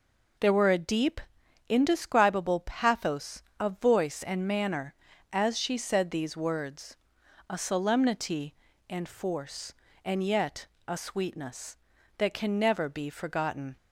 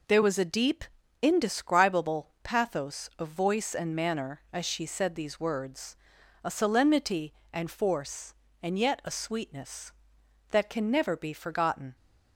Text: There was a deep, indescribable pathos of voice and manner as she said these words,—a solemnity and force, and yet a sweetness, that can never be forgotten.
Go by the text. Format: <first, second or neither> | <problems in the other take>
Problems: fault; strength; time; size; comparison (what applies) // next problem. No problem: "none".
second | says "were" for "was"; at 0.5 s // pauses between "yet" and "a"; slight; at 10.6 s; 0.22 s long